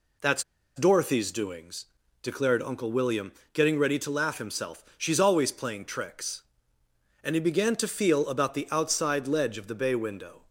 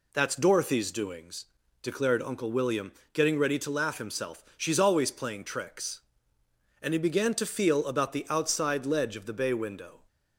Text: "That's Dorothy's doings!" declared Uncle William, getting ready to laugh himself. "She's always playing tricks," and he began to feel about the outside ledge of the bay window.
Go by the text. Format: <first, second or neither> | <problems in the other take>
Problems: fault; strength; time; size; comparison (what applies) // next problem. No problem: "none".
second | pauses between "That's" and "Dorothy's"; slight; at 0.4 s; 0.35 s long